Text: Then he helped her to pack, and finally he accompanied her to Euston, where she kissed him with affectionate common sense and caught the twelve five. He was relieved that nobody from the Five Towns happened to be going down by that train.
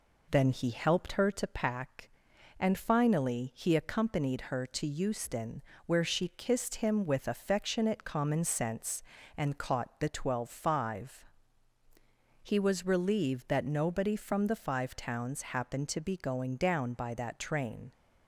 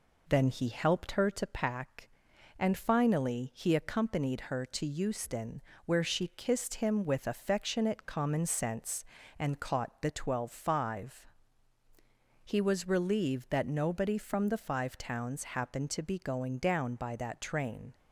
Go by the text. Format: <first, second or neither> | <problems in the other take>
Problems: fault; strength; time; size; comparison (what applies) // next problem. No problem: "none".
neither | none